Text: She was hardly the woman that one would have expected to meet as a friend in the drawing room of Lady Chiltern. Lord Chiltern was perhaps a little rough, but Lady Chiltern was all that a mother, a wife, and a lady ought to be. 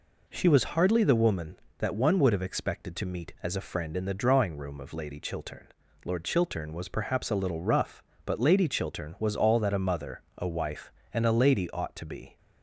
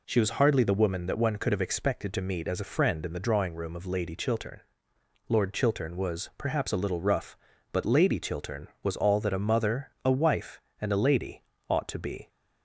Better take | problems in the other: first | says "could" for "would"; at 1.3 s // pauses between "lady" and "ought"; slight; at 11.4 s; 0.28 s long

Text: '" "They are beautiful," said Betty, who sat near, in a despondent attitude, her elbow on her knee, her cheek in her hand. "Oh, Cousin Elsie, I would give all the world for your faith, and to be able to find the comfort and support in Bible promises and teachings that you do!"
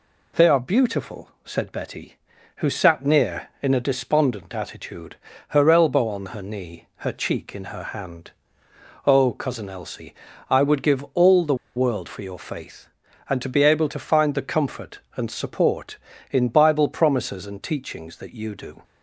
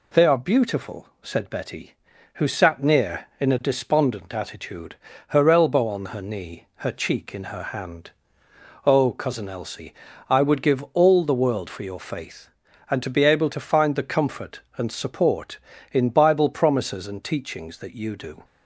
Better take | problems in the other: second | pauses between "the" and "world"; slight; at 11.5 s; 0.21 s long

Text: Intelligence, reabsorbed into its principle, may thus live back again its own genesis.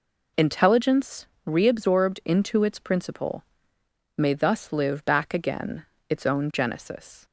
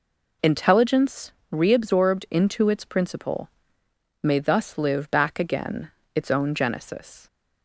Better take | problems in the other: neither | pauses between "again" and "its"; slight; the same in both

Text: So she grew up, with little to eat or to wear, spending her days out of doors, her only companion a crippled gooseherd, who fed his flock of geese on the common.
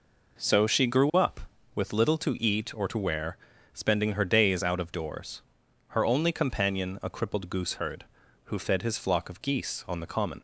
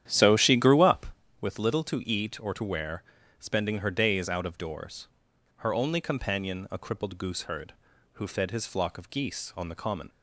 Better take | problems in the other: first | starts louder than the rest; strong; until 1.1 s; 10.5 dB

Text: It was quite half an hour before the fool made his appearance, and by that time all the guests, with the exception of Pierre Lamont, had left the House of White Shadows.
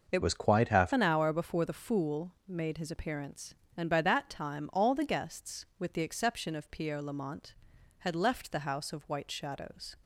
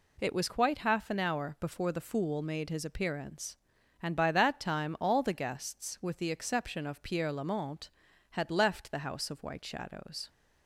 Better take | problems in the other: second | changes voice from "was" to "half"; from 0.2 to 0.9 s; 0.7 s long // pauses between "fool" and "made"; slight; at 2.3 s; 0.16 s long

